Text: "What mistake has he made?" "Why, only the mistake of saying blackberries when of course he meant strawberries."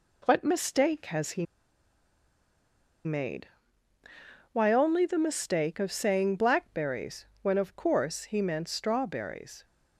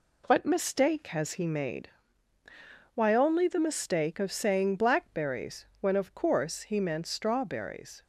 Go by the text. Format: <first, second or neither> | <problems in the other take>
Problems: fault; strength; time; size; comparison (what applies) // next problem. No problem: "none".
second | pauses between "he" and "made"; strong; at 1.4 s; 1.6 s long // pauses between "blackberries" and "when"; slight; at 7.2 s; 0.16 s long